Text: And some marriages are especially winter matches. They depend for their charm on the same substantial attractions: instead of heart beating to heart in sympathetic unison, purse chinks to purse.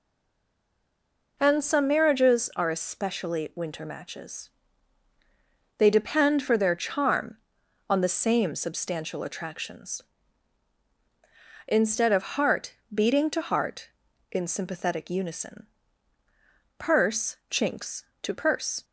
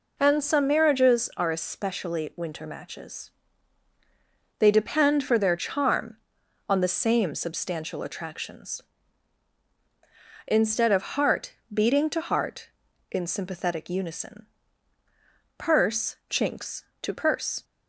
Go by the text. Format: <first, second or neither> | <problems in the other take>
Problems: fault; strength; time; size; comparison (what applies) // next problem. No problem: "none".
second | stays silent before the first word; noticeable; until 1.3 s; 1.3 s long // pauses between "heart" and "beating"; slight; at 12.7 s; 0.20 s long; slight in the second